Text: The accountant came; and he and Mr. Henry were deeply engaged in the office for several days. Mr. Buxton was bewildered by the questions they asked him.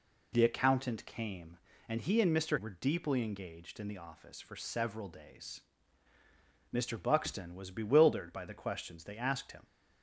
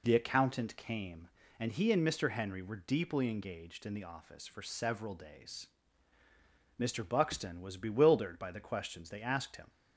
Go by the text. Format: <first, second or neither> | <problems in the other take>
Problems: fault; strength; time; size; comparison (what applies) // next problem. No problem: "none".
second | skips "Henry"; at 2.5 s